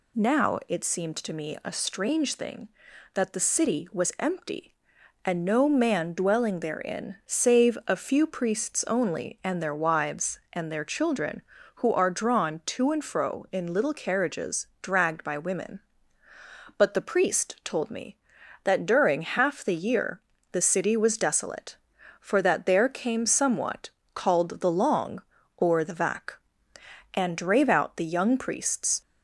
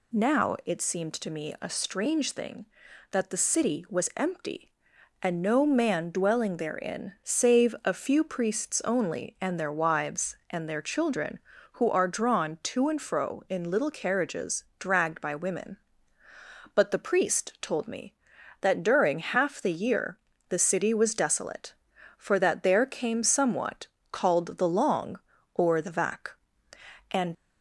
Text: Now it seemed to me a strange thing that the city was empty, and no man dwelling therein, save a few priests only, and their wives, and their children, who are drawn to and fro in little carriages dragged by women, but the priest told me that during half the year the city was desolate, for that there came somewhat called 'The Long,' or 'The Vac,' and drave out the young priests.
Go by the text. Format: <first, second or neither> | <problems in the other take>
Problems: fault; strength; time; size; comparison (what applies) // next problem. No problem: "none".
first | pauses between "year" and "the"; slight; at 20.1 s; 0.30 s long; slight in the first // pauses between "somewhat" and "called"; slight; at 23.8 s; 0.24 s long; slight in the first // stops before "drave out the young priests"; at 27.3 s